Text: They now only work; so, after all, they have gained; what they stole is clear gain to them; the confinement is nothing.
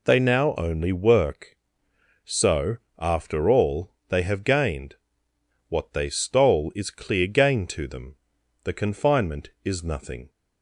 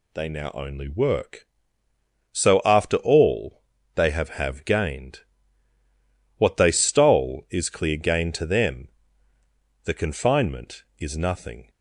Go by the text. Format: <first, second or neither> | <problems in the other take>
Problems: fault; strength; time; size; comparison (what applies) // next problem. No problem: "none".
first | says "have" twice; at 4.2 s